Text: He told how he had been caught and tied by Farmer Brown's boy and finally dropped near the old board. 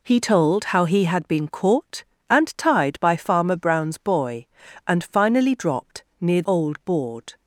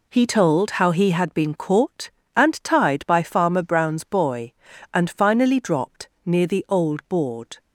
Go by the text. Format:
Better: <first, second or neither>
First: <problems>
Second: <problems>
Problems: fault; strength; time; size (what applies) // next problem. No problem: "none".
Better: second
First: pauses between "dropped" and "near"; slight; at 6.0 s; 0.18 s long // skips "the"; at 6.4 s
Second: pauses between "dropped" and "near"; slight; at 6.0 s; 0.18 s long